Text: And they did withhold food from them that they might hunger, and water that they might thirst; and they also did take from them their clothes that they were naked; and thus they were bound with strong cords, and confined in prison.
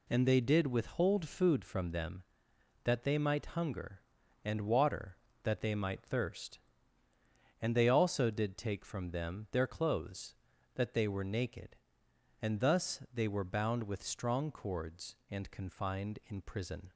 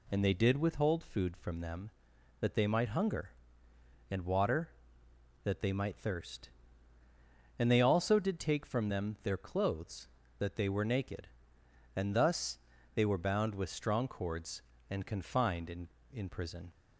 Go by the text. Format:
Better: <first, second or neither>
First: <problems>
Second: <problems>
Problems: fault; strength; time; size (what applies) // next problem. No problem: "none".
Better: first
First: none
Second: pauses between "thus" and "they"; slight; at 12.5 s; 0.36 s long // says "in" twice; at 16.1 s